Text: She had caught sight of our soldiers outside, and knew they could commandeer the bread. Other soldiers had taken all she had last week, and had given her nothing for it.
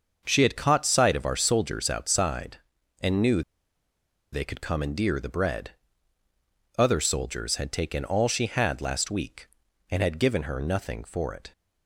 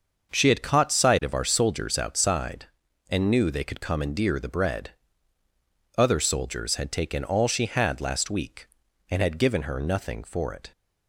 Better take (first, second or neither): second